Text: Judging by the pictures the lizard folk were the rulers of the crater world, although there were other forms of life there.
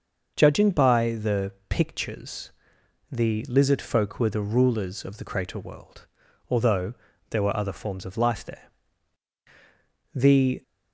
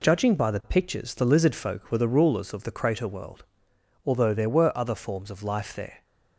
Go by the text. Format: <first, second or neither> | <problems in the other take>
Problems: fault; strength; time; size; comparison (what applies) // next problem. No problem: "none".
second | starts louder than the rest; noticeable; until 1.3 s; 6 dB // pauses between "the" and "pictures"; slight; at 1.5 s; 0.18 s long // pauses between "pictures" and "the"; noticeable; at 2.4 s; 0.60 s long // pauses between "although" and "there"; slight; at 6.9 s; 0.36 s long // goes on to say "The"; slight; from 10.1 s on; 0.48 s long